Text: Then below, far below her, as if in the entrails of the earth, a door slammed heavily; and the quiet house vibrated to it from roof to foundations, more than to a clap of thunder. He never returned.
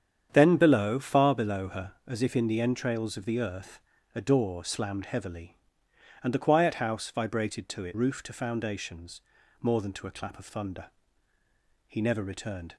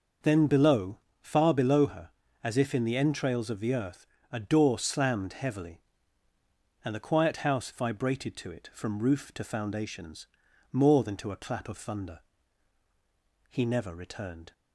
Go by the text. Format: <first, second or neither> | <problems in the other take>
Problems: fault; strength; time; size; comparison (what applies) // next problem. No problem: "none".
second | starts louder than the rest; strong; until 1.3 s; 8.5 dB // skips "from"; at 7.9 s